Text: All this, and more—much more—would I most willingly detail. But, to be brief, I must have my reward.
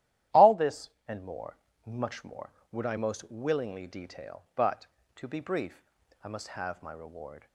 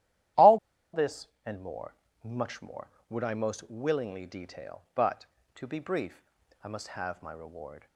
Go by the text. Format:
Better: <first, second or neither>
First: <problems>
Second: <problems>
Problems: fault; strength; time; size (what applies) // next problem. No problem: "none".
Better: first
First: starts louder than the rest; strong; until 1.5 s; 12.5 dB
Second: starts louder than the rest; strong; until 1.9 s; 12.5 dB // pauses between "All" and "this"; at 0.5 s; 0.37 s long